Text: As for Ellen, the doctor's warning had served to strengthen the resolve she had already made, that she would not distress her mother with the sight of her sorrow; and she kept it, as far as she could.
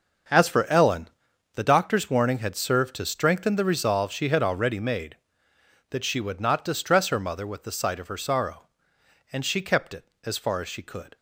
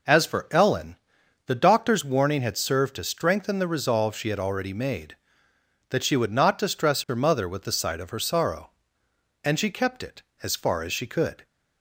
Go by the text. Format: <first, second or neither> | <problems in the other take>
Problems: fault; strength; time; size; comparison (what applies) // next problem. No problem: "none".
second | gets quieter; strong; throughout; 12 dB